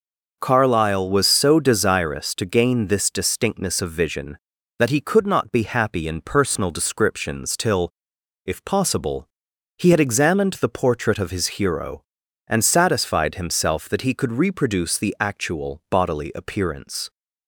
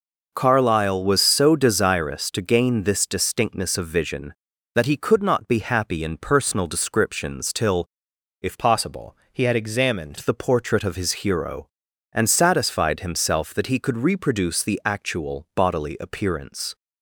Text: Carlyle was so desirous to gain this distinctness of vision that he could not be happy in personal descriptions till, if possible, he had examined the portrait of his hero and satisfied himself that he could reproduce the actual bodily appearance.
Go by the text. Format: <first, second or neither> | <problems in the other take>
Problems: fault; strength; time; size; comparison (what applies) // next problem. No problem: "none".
first | changes voice from "possible" to "examined"; from 8.5 to 10.1 s; 1.6 s long